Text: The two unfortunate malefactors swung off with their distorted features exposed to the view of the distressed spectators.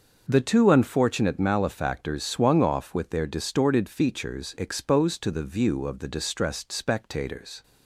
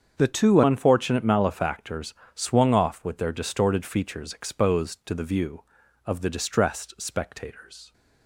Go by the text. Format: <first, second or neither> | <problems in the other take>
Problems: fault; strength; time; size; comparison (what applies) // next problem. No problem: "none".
first | starts louder than the rest; until 1.2 s; 7 dB; noticeable in the first // changes voice at "unfortunate"; from 0.6 s on; 7.3 s long // pauses between "malefactors" and "swung"; slight; at 2.1 s; 0.22 s long